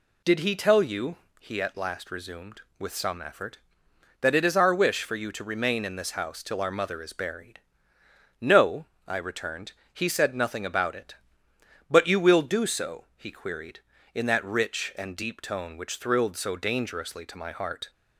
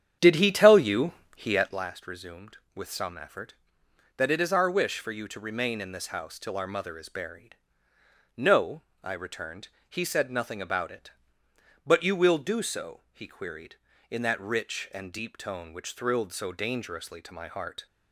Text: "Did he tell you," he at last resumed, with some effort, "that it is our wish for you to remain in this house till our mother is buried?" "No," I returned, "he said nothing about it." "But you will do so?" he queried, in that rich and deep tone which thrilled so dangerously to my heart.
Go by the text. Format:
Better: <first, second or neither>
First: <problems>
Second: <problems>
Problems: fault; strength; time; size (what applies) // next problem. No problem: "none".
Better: first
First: none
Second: starts louder than the rest; strong; until 1.8 s; 9 dB